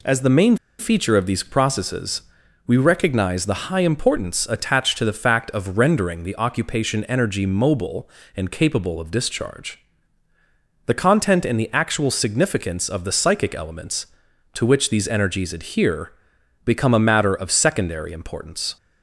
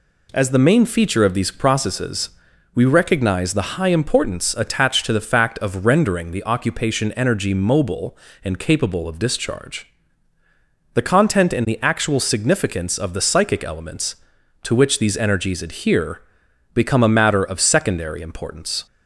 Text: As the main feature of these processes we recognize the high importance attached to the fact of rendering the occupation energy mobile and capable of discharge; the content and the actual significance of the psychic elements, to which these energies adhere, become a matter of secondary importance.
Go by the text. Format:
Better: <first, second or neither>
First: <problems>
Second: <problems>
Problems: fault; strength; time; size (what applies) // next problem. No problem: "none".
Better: second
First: pauses between "main" and "feature"; slight; at 0.5 s; 0.23 s long // pauses between "processes" and "we"; at 2.2 s; 0.42 s long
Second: pauses between "processes" and "we"; at 2.3 s; 0.42 s long